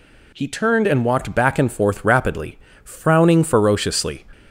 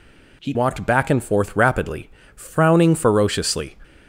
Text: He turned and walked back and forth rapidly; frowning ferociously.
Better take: first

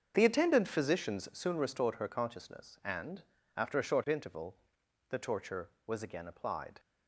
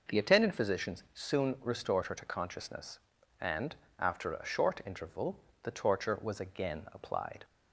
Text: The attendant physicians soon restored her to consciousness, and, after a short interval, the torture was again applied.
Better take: second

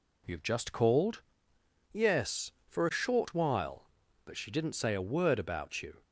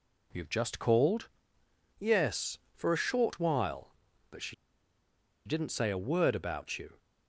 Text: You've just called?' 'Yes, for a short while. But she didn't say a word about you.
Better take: first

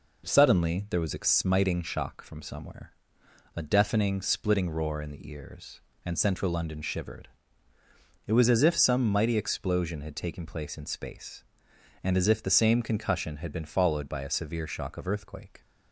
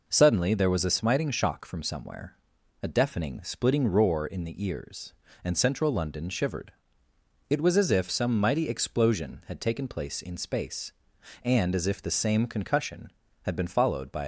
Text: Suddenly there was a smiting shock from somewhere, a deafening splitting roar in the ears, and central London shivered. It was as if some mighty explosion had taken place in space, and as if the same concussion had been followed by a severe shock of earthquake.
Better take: first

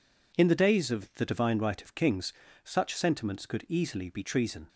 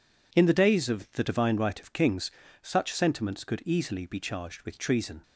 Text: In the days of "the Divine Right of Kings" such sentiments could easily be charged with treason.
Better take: second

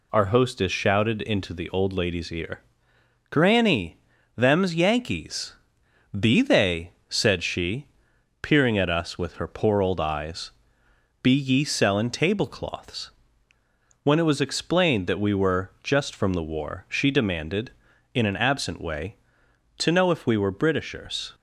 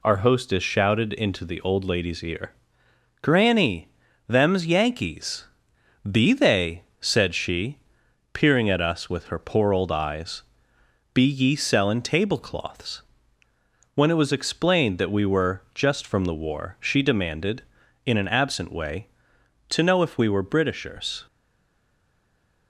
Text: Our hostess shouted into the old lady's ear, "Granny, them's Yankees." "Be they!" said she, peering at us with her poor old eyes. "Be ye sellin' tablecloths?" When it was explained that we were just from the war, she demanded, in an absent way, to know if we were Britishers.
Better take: first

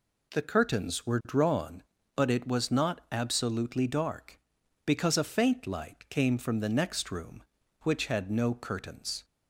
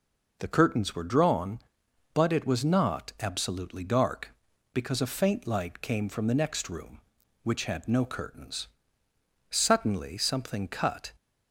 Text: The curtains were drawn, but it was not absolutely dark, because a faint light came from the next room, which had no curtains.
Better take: first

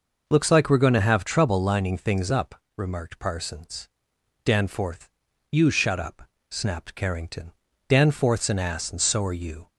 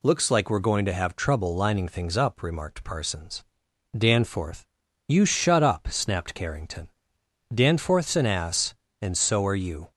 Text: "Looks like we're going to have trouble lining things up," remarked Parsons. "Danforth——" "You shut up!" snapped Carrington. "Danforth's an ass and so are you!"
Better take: neither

